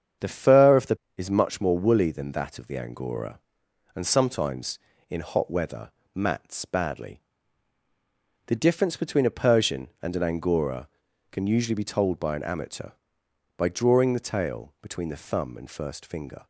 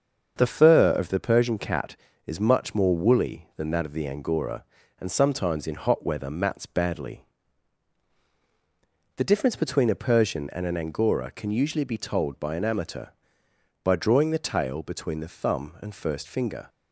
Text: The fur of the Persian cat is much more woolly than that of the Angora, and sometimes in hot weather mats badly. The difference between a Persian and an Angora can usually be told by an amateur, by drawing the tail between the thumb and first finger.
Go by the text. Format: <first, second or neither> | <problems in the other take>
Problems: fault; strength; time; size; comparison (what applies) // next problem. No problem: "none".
second | starts louder than the rest; strong; until 1.4 s; 8 dB; also in the second // skips "Persian cat"; at 1.0 s // pauses between "weather" and "mats"; slight; at 5.8 s; 0.24 s long